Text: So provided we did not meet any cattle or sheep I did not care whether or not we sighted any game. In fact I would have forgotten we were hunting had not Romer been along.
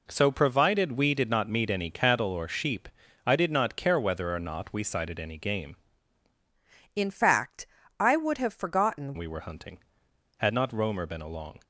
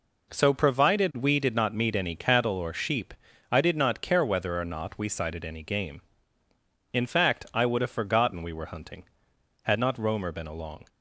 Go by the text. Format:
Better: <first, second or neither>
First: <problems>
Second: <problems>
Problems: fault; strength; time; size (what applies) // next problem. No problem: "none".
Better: second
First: pauses between "sheep" and "I"; at 2.8 s; 0.38 s long // changes voice from "In" to "forgotten"; from 6.9 to 9.1 s; 2.2 s long // pauses between "fact" and "I"; slight; at 7.6 s; 0.32 s long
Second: pauses between "sheep" and "I"; at 3.1 s; 0.38 s long